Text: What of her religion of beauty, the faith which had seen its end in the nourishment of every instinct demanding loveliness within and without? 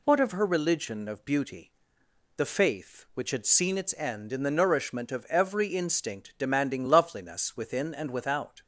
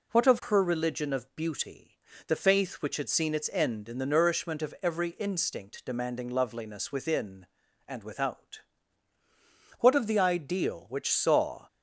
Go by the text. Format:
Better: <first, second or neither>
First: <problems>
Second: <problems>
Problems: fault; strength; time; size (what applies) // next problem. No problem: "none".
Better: first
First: none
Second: goes on to say "What of the ideal which saw"; strong; from 9.7 s on; 1.8 s long